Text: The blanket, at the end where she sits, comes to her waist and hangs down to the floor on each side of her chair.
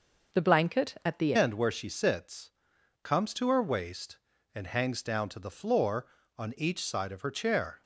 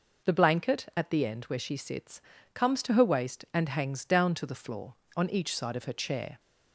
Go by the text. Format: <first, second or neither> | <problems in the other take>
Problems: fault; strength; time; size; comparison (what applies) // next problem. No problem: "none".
second | starts louder than the rest; noticeable; until 1.4 s; 6 dB // changes voice at "end"; from 1.3 s on; 6.5 s long